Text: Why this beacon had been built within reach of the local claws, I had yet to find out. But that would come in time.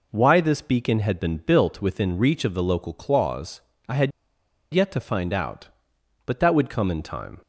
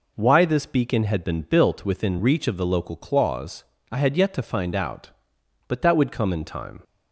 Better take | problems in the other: second | pauses between "had" and "yet"; noticeable; at 4.1 s; 0.63 s long

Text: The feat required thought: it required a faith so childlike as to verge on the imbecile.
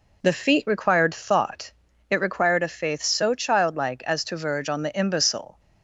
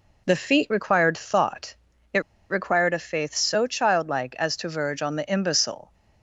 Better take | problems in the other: first | pauses between "it" and "required"; slight; at 2.2 s; 0.28 s long

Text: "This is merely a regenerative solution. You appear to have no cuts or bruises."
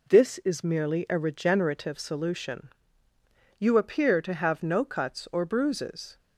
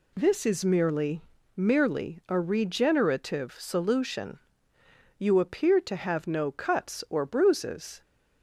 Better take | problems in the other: first | says "merely" twice; at 1.5 s

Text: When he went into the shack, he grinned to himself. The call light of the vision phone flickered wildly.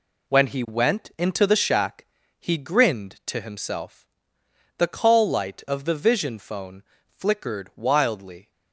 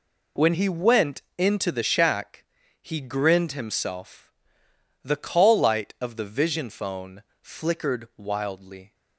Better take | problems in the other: first | pauses between "went" and "into"; slight; at 1.2 s; 0.16 s long // skips "to"; at 3.5 s // pauses between "phone" and "flickered"; slight; at 7.2 s; 0.18 s long; slight in the first

